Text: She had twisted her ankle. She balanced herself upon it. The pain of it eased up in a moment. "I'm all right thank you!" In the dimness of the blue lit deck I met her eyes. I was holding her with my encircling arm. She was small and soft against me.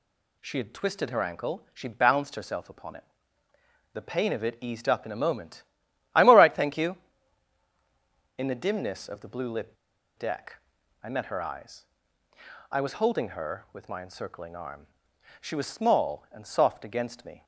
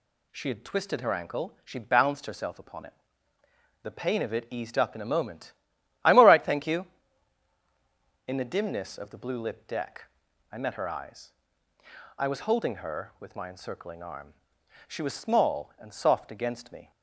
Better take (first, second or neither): second